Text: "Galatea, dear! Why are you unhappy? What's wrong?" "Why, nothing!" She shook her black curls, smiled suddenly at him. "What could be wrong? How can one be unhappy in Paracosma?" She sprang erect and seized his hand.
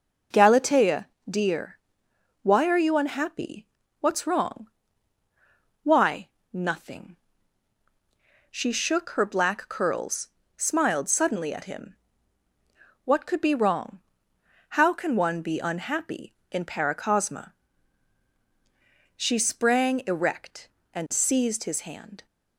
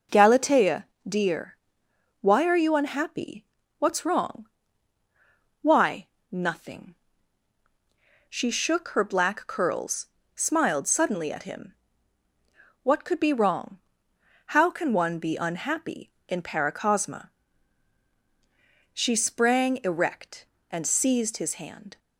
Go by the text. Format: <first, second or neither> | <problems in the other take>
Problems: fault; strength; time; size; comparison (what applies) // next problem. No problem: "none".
neither | none